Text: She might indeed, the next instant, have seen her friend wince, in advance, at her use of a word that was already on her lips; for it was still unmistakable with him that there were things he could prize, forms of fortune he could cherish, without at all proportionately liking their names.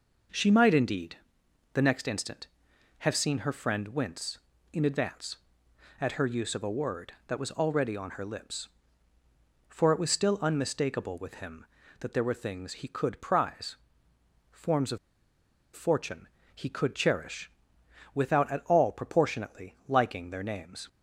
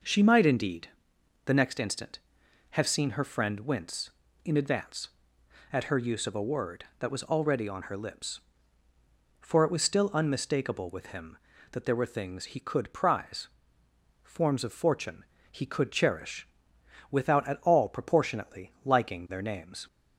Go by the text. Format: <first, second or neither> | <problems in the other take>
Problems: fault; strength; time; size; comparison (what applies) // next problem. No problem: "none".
second | pauses between "of" and "fortune"; noticeable; at 14.9 s; 0.77 s long // pauses between "fortune" and "he"; slight; at 16.2 s; 0.28 s long; slight in the second